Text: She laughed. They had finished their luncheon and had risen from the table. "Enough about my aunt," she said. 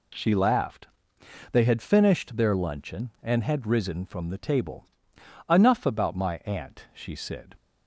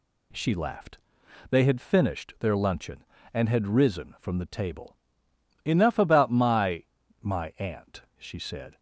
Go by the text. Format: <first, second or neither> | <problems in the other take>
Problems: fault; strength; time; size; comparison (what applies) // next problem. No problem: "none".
first | says "my" twice; at 7.1 s